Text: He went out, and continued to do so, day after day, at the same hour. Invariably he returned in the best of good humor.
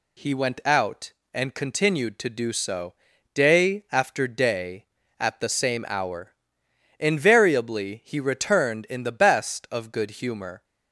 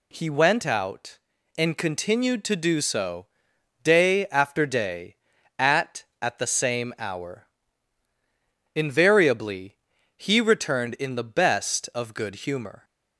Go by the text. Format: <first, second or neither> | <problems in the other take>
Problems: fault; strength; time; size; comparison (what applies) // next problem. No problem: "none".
first | says "at" twice; at 6.1 s // pauses between "Invariably" and "he"; at 9.7 s; 0.42 s long